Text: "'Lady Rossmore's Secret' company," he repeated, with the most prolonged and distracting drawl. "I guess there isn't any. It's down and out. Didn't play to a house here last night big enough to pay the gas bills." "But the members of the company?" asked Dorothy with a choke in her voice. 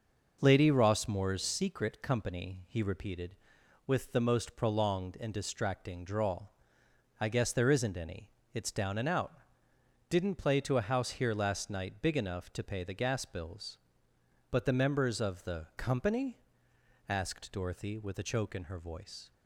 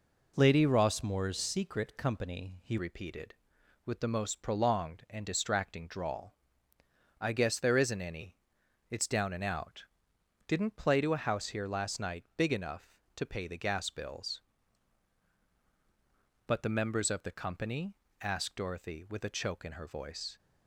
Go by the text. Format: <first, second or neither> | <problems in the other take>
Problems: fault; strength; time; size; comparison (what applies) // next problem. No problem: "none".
first | changes voice at "repeated"; from 2.7 s on; 17.6 s long